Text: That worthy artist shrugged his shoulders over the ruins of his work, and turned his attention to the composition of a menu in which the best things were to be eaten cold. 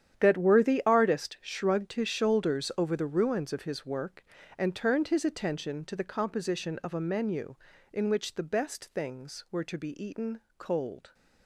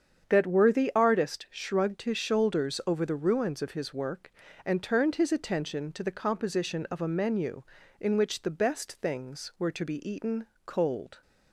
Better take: second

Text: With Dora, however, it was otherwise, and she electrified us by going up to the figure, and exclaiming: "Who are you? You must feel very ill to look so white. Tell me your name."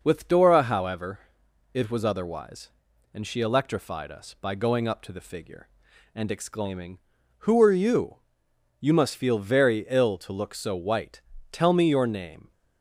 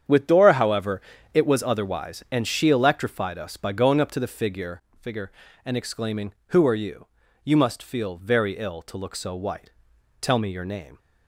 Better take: first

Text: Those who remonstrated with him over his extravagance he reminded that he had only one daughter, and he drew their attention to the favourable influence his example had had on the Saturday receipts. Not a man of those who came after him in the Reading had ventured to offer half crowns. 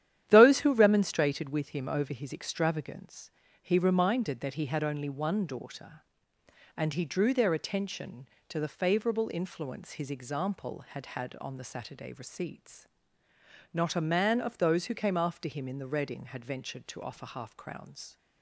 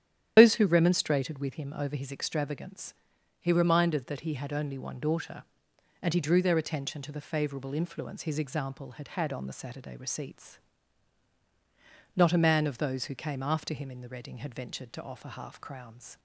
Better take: first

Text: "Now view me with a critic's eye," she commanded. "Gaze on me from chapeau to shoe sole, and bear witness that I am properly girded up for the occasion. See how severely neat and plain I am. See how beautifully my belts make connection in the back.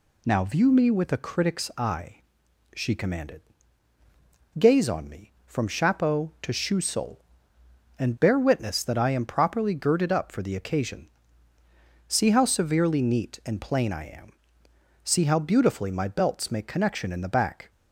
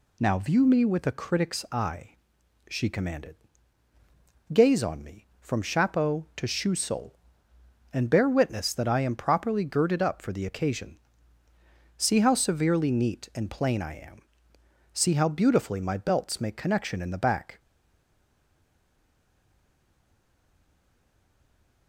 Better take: first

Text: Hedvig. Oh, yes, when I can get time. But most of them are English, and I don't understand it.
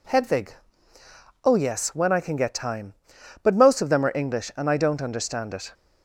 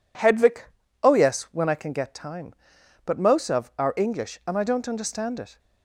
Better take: first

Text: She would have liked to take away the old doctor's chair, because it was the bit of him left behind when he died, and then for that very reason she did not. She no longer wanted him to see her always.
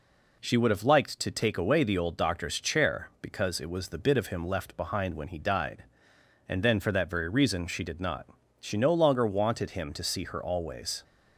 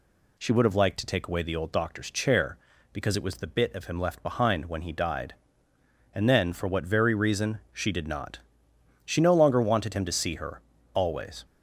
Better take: first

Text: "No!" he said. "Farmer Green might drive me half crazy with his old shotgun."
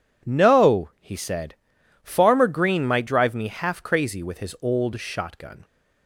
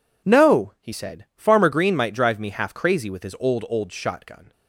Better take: first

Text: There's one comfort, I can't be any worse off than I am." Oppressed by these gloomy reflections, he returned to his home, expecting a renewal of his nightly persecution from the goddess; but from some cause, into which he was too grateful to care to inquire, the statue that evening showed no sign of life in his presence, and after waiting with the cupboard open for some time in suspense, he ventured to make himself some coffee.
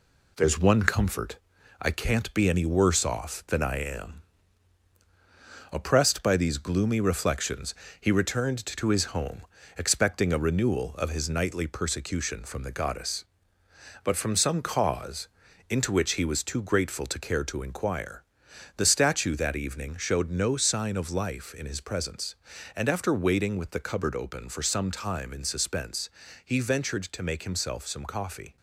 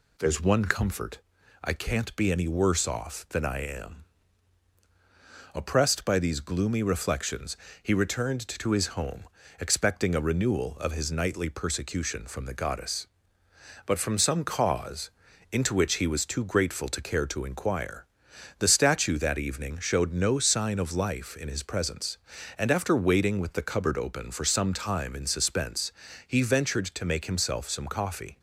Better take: second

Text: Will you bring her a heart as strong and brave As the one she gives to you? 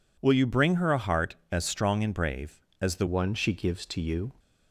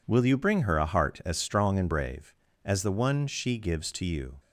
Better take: second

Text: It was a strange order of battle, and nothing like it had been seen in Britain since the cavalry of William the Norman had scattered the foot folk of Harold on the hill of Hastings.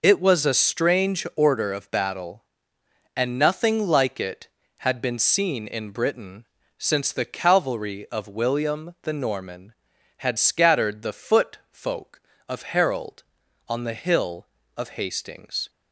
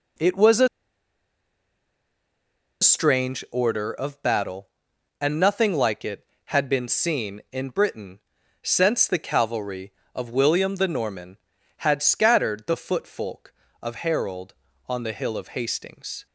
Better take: first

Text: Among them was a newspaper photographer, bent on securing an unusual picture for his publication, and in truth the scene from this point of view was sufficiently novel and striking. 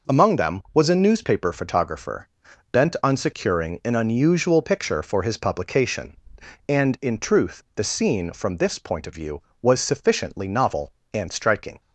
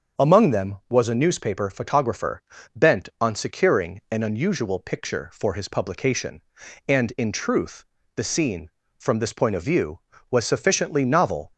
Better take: first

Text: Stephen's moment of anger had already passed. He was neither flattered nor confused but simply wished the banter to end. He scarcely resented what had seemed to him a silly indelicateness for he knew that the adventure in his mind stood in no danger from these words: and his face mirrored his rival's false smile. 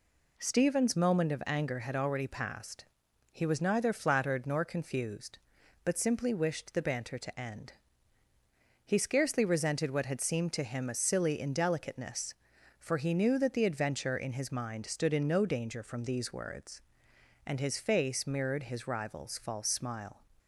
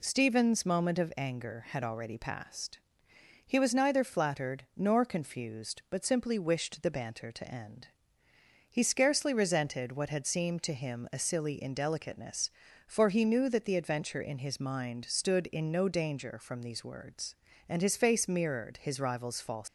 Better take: first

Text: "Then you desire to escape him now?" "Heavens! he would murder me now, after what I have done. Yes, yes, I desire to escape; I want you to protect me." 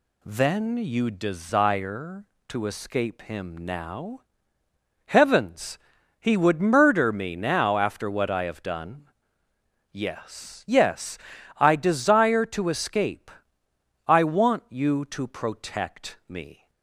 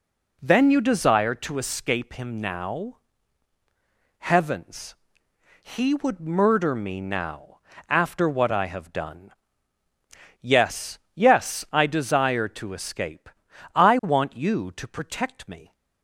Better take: neither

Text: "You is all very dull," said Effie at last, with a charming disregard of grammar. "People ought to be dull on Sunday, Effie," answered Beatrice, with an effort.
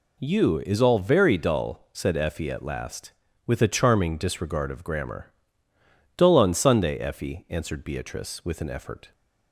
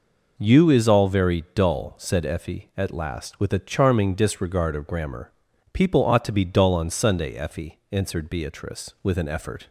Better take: second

